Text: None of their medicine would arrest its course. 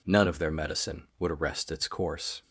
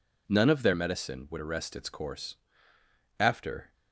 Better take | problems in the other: first | goes on to say "After"; from 3.1 s on; 0.54 s long

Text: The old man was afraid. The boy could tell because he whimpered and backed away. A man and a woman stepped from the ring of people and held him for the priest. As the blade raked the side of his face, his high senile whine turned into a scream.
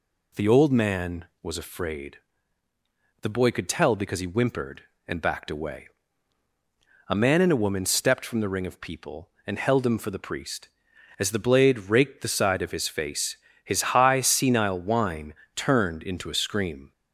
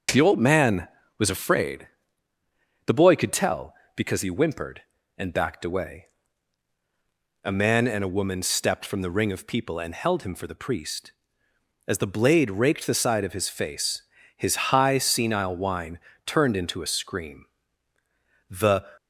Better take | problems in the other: first | starts louder than the rest; until 1.4 s; 6.5 dB // pauses between "whine" and "turned"; slight; at 15.9 s; 0.26 s long; slight in the first // goes on to say "The"; slight; from 18.4 s on; 0.36 s long

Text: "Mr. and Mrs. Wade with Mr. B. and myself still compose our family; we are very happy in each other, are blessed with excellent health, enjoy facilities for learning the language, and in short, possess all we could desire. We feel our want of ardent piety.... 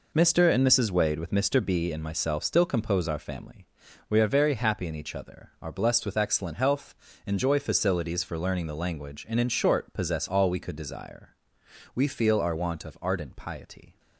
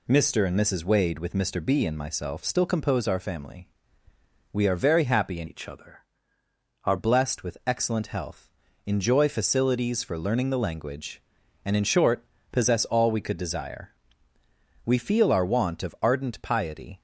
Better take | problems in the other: first | changes voice from "each" to "are"; from 5.4 to 6.9 s; 1.5 s long

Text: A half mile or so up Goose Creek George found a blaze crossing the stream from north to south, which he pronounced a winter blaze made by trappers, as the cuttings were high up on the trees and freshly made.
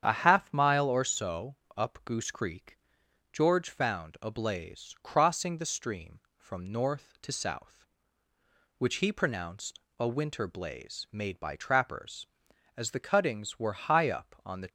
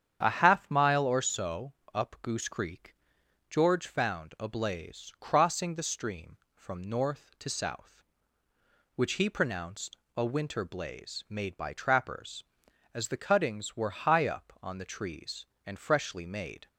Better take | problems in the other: second | starts louder than the rest; strong; until 1.0 s; 9 dB; strong in the second // pauses between "so" and "up"; slight; at 1.5 s; 0.22 s long; slight in the second // pauses between "Creek" and "George"; noticeable; at 2.7 s; 0.56 s long; noticeable in the second // pauses between "pronounced" and "a"; slight; at 9.8 s; 0.18 s long; slight in the second // stops before "trees and freshly made"; at 14.6 s

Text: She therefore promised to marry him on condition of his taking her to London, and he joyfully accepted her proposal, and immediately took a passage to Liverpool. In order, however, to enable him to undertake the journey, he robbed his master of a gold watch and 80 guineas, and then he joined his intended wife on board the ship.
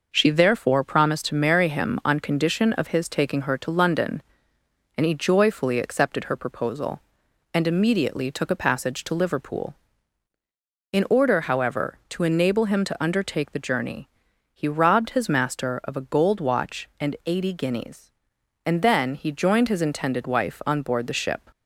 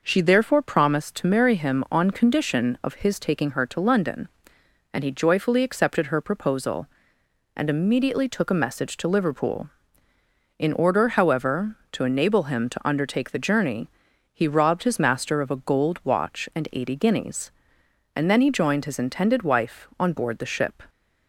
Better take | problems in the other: first | says "message" for "passage"; at 8.6 s

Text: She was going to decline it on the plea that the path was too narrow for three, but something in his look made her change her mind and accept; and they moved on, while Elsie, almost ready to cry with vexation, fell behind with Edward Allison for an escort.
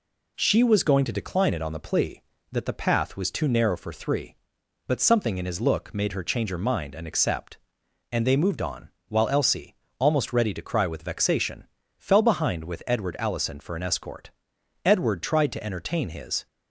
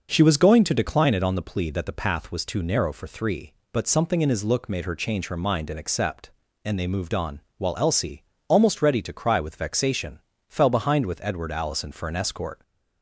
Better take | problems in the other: second | goes on to say "Edward tried to entertain his"; from 14.8 s on; 1.6 s long

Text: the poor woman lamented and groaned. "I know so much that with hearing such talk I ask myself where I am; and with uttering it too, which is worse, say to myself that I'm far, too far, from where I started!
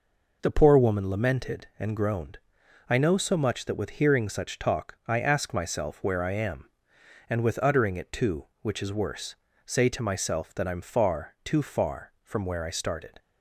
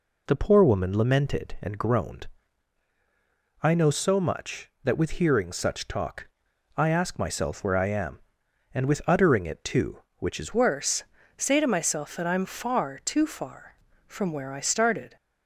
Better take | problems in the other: first | pauses between "talk" and "I"; noticeable; at 6.2 s; 0.48 s long // changes voice at "worse"; from 10.5 s on; 4.6 s long

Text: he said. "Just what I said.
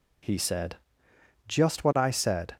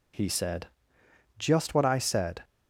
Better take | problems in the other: neither | none

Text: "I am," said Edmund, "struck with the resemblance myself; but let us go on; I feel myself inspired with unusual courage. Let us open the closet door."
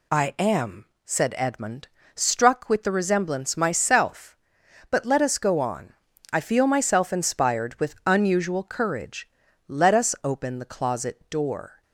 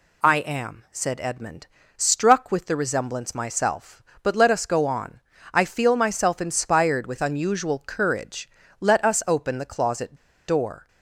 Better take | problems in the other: first | pauses between "closet" and "door"; slight; at 10.1 s; 0.32 s long

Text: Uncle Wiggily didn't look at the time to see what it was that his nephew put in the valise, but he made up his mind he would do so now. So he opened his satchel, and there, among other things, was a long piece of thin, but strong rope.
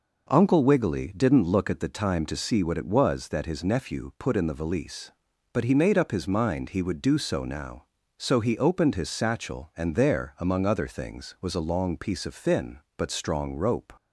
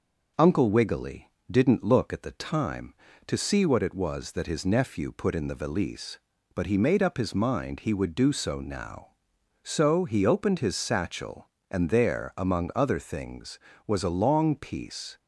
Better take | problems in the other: first | pauses between "Wiggily" and "didn't"; slight; at 1.2 s; 0.18 s long // stops before "of thin but strong rope"; at 15.1 s

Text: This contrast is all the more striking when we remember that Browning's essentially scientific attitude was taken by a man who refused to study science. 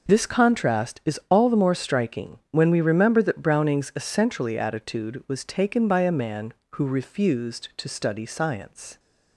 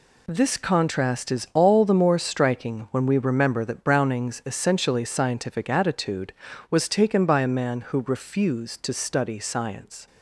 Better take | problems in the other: second | skips "scientific"; at 4.5 s

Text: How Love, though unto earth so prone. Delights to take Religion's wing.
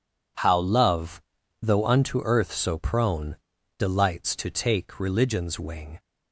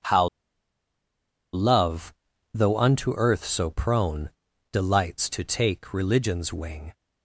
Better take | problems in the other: first | pauses between "How" and "Love"; strong; at 0.2 s; 1.2 s long

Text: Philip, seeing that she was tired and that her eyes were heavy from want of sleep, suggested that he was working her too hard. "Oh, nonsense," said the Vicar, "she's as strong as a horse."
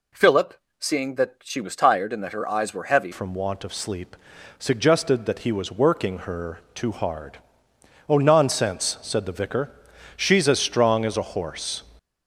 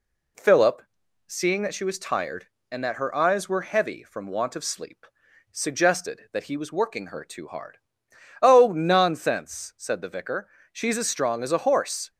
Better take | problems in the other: second | changes voice at "from"; from 3.1 s on; 8.7 s long

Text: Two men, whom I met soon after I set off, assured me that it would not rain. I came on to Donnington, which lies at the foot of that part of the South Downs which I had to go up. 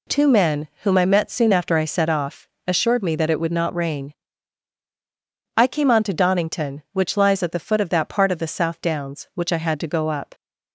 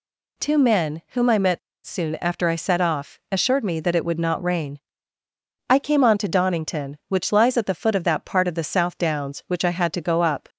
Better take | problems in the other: first | pauses between "met" and "soon"; slight; at 1.5 s; 0.27 s long

